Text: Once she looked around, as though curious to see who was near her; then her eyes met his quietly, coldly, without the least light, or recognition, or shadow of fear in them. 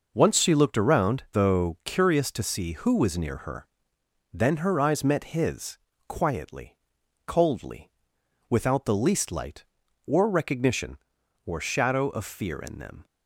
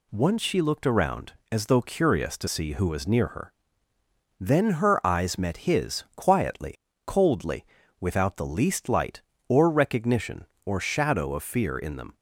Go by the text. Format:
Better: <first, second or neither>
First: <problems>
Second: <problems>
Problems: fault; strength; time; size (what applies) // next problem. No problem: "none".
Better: second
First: skips "as"; at 1.2 s // pauses between "his" and "quietly"; slight; at 5.7 s; 0.30 s long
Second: none